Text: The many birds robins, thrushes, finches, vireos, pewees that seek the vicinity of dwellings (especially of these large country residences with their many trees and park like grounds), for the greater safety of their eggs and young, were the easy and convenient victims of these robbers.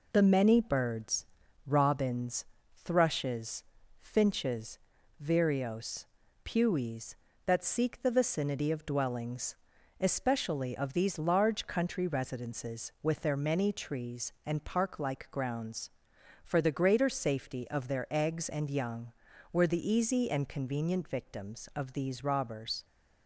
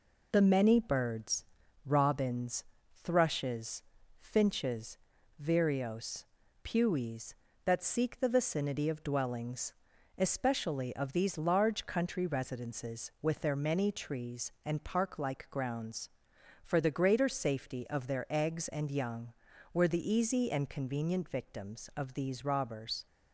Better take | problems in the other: neither | pauses between "birds" and "robins"; the same in both

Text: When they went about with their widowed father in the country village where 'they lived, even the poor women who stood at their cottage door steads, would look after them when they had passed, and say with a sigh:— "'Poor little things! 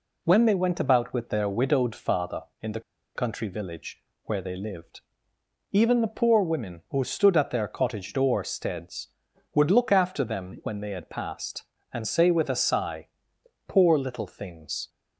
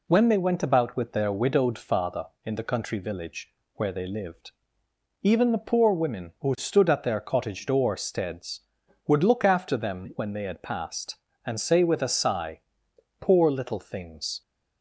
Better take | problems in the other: second | pauses between "the" and "country"; slight; at 2.8 s; 0.35 s long // pauses between "village" and "where"; slight; at 4.0 s; 0.22 s long; slight in the second

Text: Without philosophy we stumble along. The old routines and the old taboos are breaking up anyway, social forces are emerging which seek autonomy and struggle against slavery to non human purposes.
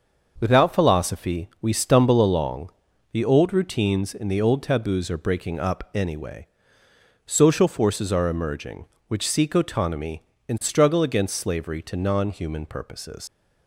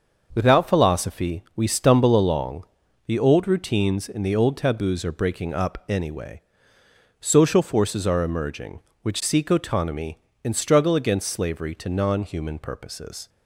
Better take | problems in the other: second | starts louder than the rest; until 1.3 s; 6 dB; also in the second // leaves "purposes" unfinished; at 13.2 s; 85 ms

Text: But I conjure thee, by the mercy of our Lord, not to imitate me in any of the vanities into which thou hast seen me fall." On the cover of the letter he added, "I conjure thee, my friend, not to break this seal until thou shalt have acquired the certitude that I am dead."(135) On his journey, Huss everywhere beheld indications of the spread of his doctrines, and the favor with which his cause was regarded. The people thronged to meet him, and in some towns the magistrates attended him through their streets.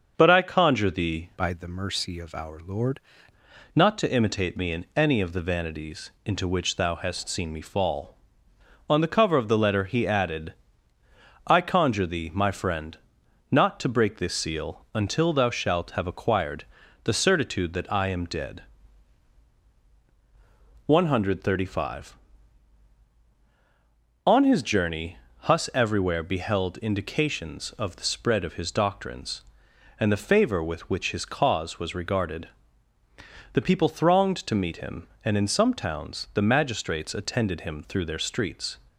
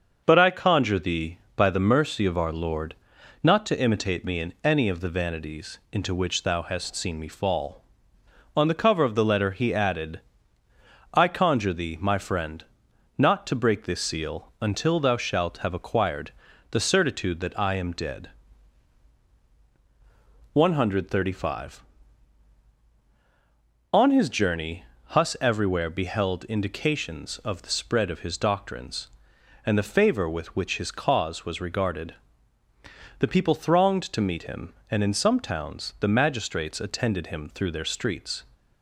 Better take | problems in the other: second | starts louder than the rest; until 1.1 s; 6.5 dB; also in the second // changes voice from "by" to "Lord"; from 1.3 to 2.9 s; 1.6 s long // pauses between "acquired" and "the"; at 16.6 s; 0.40 s long; also in the second

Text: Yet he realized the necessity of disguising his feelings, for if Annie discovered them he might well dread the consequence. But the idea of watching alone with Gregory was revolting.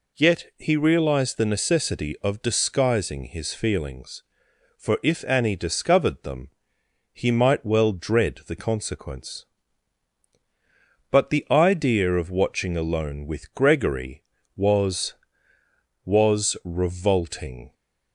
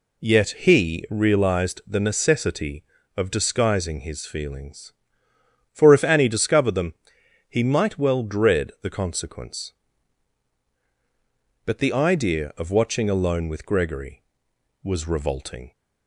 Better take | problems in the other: second | pauses between "them" and "he"; noticeable; at 6.4 s; 0.66 s long; noticeable in the second // says "was" twice; at 16.0 s

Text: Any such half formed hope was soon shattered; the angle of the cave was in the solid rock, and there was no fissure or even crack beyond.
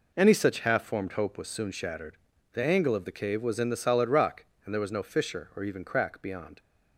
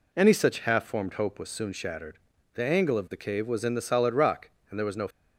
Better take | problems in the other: first | stops before "fissure or even crack beyond"; at 5.0 s

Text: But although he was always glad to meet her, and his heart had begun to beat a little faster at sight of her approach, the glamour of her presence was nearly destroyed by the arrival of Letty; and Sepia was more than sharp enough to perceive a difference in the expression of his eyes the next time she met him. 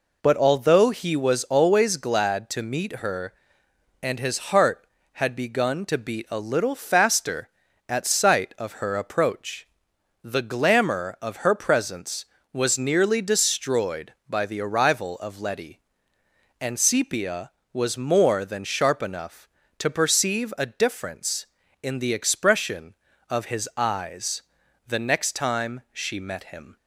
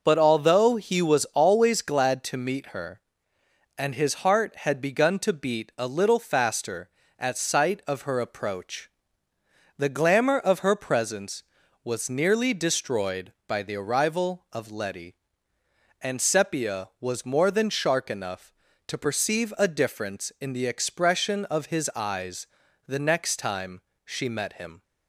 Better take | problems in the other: first | says "shark" for "sharp"; at 17.6 s // pauses between "eyes" and "the"; at 22.4 s; 0.40 s long; also in the first // pauses between "time" and "she"; slight; at 23.8 s; 0.22 s long

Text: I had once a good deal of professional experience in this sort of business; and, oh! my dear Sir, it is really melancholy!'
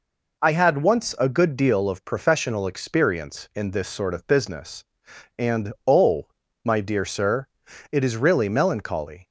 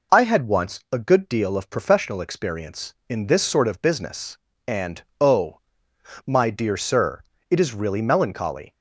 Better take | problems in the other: neither | none

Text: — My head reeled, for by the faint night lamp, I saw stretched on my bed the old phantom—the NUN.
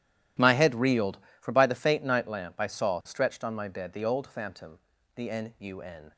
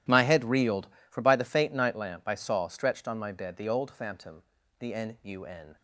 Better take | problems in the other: neither | none

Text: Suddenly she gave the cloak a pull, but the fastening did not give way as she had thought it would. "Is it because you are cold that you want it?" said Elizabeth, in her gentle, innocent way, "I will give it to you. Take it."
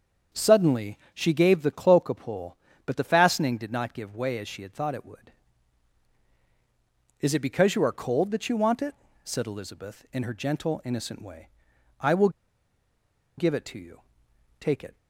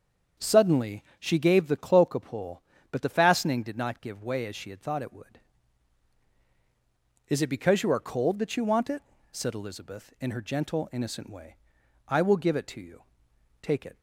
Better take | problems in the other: second | starts louder than the rest; until 1.4 s; 7 dB; also in the second // pauses between "Suddenly" and "she"; slight; at 0.9 s; 0.16 s long; slight in the second // pauses between "will" and "give"; at 12.2 s; 1.0 s long

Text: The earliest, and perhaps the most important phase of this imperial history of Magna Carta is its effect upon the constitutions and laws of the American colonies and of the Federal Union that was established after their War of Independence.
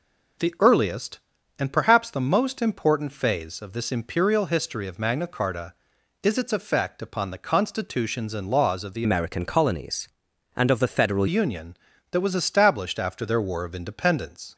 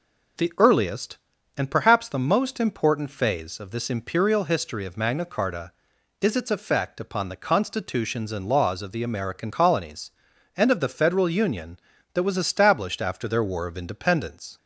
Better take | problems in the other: second | changes voice from "American" to "Federal"; from 9.0 to 11.2 s; 2.2 s long

